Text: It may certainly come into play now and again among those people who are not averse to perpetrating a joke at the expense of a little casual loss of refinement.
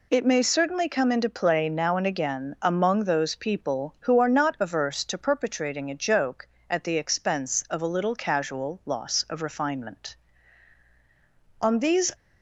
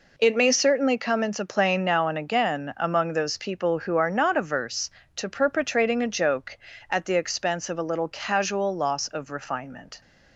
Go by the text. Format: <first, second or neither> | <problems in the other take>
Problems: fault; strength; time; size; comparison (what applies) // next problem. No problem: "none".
second | goes on to say "On these"; from 11.5 s on; 0.54 s long